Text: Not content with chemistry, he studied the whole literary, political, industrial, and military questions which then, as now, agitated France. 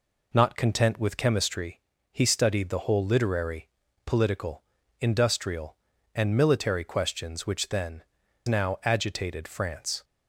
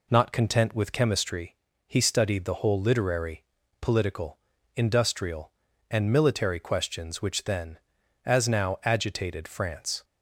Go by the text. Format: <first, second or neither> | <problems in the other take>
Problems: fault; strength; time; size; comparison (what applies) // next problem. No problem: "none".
second | skips "as"; at 8.2 s